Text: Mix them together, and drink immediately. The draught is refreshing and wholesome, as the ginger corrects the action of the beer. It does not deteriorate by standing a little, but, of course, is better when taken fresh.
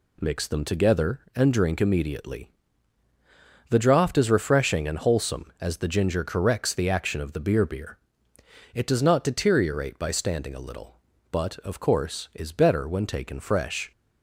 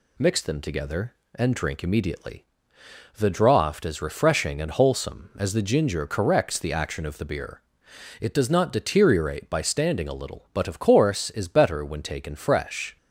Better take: second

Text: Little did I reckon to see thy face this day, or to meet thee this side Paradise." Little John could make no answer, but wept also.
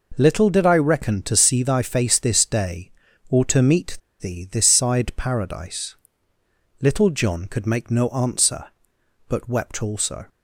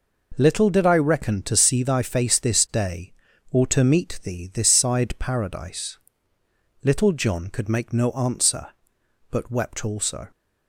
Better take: second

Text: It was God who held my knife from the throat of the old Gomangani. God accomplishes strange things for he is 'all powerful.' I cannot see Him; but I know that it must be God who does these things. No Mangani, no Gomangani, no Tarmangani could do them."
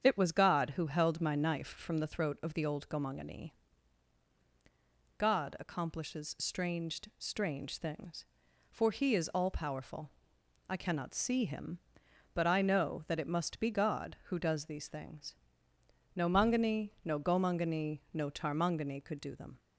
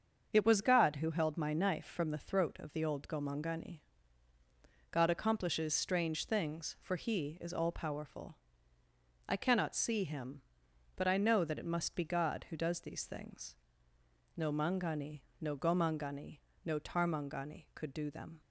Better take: second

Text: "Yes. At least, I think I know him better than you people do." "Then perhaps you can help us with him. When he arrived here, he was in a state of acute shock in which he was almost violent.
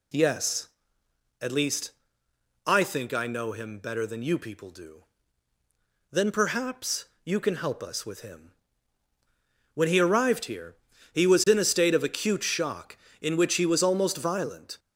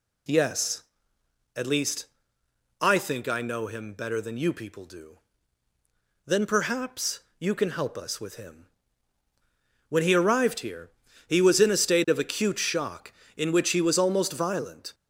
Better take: neither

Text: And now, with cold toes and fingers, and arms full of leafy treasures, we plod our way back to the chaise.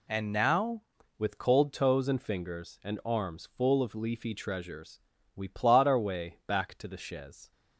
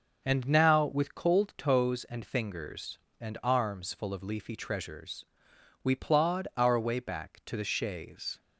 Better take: second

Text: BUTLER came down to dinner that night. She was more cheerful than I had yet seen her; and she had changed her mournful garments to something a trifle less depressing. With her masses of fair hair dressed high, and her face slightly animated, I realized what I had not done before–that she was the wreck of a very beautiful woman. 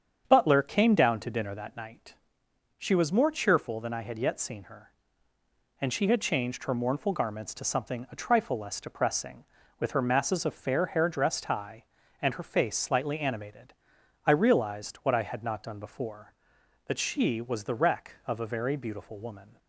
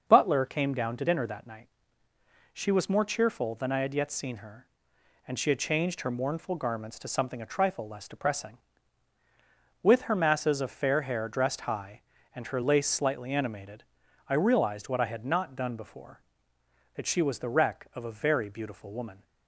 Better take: first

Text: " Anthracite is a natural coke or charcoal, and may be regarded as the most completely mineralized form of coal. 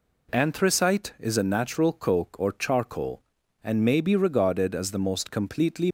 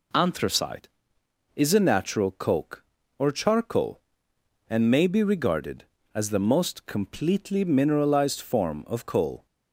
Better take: second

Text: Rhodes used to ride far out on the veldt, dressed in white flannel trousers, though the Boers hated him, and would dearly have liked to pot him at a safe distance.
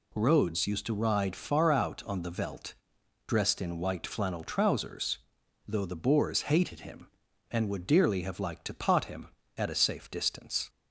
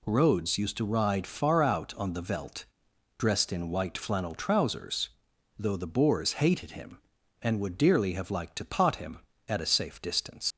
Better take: first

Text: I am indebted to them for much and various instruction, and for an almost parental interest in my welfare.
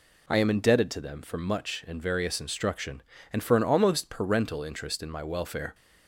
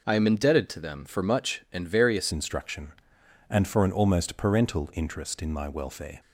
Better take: first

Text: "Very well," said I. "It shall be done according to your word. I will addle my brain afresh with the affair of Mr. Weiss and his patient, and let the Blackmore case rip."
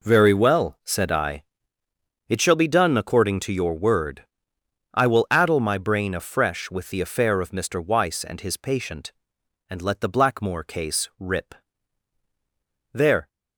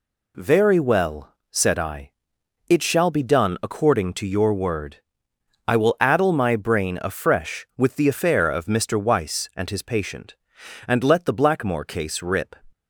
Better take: second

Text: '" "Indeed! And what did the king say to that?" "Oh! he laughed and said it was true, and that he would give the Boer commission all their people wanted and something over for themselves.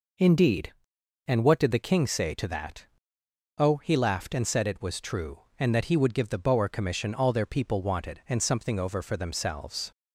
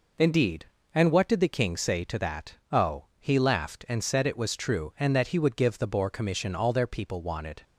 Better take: first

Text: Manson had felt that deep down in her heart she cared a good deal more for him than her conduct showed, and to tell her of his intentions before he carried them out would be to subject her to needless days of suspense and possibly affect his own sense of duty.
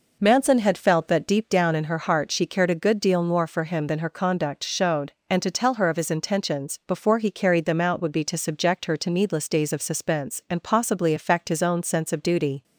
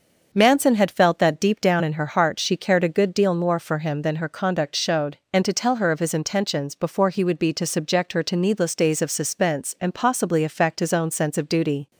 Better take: first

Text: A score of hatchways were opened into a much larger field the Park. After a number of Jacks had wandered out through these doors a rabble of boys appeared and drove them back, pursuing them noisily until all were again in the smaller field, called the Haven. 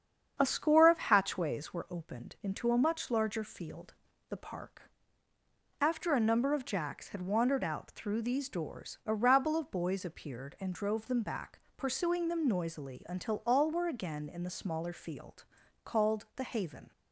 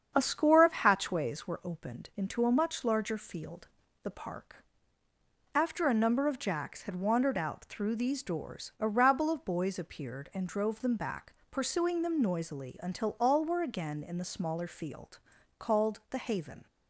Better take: neither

